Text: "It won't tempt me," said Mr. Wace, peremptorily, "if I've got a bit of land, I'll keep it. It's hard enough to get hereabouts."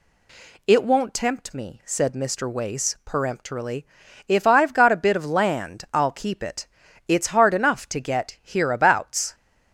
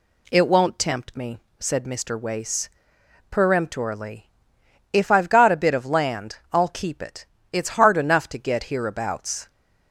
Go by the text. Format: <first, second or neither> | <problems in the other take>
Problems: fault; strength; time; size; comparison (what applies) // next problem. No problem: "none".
neither | none